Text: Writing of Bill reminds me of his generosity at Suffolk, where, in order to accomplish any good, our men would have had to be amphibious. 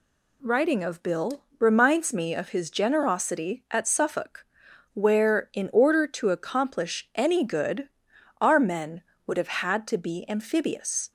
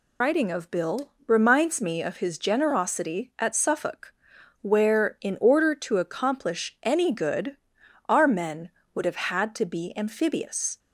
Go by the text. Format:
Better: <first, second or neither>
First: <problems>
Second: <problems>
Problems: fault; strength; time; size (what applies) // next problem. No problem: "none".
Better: first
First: pauses between "Bill" and "reminds"; slight; at 1.4 s; 0.16 s long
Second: loses the start of "Writing"; at 0.2 s; 115 ms // pauses between "Bill" and "reminds"; slight; at 1.1 s; 0.16 s long